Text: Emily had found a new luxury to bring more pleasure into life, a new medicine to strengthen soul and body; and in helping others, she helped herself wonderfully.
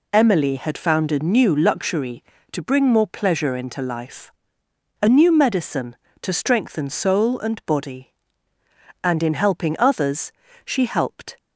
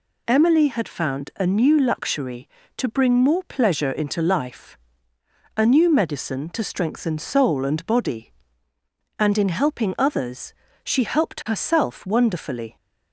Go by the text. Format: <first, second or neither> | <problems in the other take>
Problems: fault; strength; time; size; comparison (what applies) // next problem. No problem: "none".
second | stops before "herself wonderfully"; at 11.3 s